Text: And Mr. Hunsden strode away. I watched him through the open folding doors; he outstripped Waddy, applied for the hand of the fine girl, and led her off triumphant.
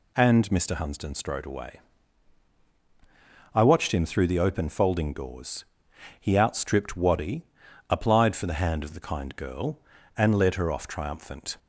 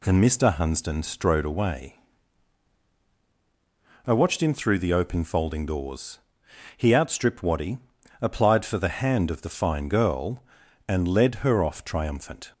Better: second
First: says "kind" for "fine"; at 8.9 s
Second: none

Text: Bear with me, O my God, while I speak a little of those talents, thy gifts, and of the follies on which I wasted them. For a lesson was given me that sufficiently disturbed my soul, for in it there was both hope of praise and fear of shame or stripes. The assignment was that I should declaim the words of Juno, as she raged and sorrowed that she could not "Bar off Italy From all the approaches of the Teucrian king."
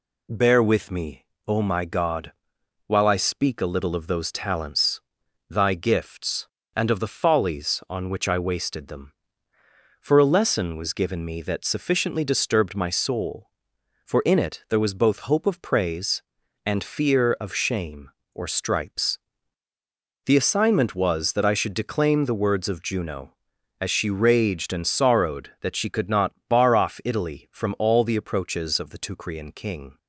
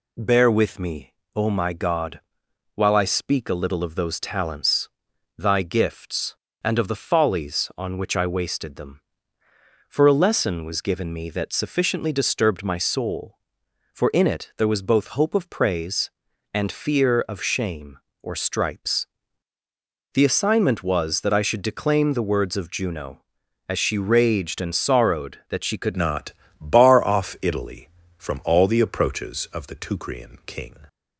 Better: first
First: pauses between "not" and "Bar"; slight; at 26.3 s; 0.16 s long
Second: changes voice at "not"; from 25.9 s on; 4.8 s long // pauses between "not" and "Bar"; slight; at 26.3 s; 0.28 s long

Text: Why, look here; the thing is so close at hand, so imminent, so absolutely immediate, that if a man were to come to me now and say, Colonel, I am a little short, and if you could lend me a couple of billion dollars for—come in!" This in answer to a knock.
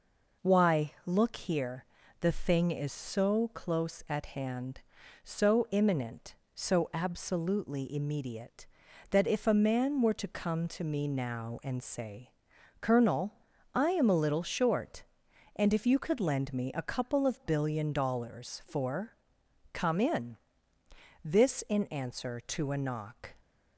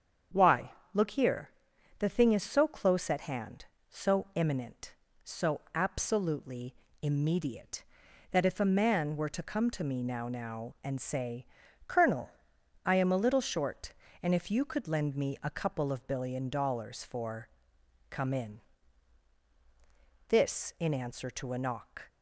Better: first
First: none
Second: starts louder than the rest; strong; until 2.0 s; 7.5 dB // pauses between "absolutely" and "immediate"; slight; at 6.7 s; 0.28 s long // says "now" twice; at 10.2 s

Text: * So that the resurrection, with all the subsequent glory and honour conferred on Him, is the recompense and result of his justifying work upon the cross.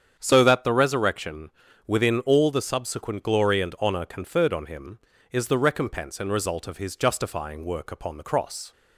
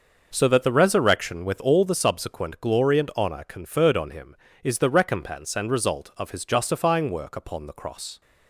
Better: second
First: starts louder than the rest; strong; until 1.2 s; 8 dB // says "within" for "with"; at 1.8 s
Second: none

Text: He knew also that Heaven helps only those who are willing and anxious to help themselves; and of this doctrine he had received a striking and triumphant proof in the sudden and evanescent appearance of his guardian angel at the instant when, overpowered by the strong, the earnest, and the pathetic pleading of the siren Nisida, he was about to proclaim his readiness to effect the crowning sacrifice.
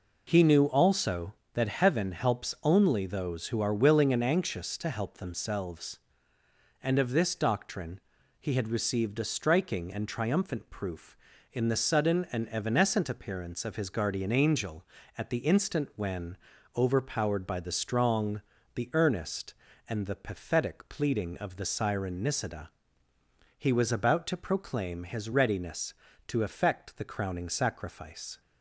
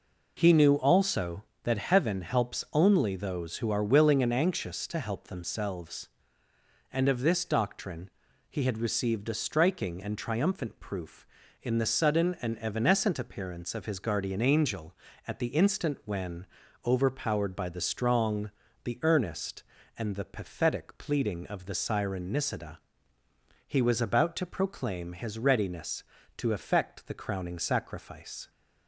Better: neither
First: pauses between "doctrine" and "he"; at 7.9 s; 0.40 s long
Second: pauses between "doctrine" and "he"; at 8.0 s; 0.40 s long

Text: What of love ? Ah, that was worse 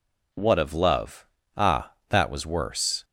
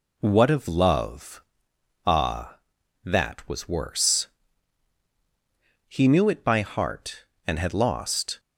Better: first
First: none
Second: goes on to say "He knew it by heart and had lost"; strong; from 5.8 s on; 2.5 s long

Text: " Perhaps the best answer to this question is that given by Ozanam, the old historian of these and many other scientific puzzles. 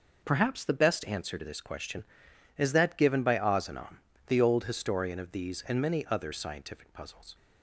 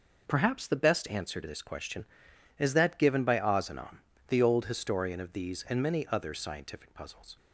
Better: neither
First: none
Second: none

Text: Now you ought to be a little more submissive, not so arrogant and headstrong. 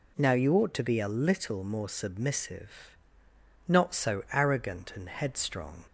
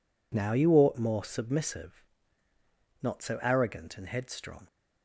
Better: first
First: none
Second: skips "to be a little"; at 0.9 s

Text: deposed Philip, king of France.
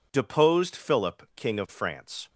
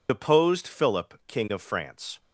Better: first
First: none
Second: loses the start of "deposed"; at 0.0 s; 65 ms

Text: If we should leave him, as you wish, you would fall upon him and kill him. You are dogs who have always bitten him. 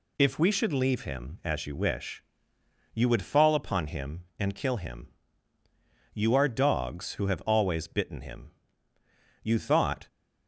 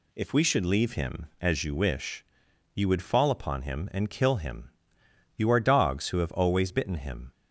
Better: second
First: goes on to say "You thought"; noticeable; from 9.4 s on; 0.64 s long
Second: none

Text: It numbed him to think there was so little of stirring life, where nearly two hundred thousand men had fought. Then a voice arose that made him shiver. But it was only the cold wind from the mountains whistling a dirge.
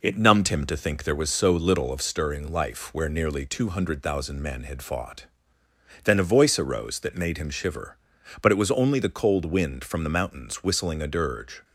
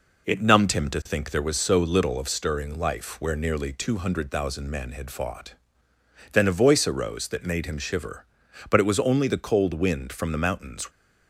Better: first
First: none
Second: stops before "whistling a dirge"; at 10.9 s

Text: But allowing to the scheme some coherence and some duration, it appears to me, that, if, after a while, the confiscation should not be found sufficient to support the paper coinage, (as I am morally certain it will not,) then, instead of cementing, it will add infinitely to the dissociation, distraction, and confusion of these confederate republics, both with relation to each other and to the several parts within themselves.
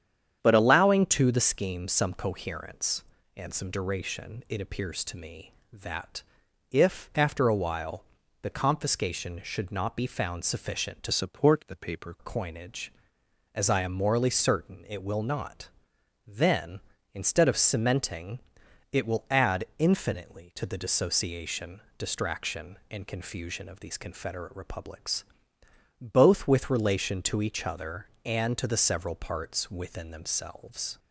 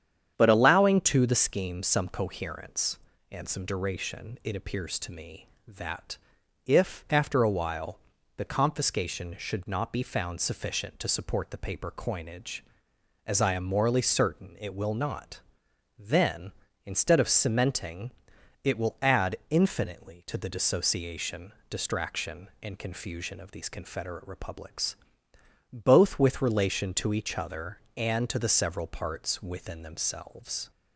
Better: second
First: starts louder than the rest; strong; until 1.4 s; 9 dB // changes voice from "support" to "paper"; from 11.1 to 12.1 s; 1.0 s long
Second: starts louder than the rest; strong; until 1.3 s; 9 dB

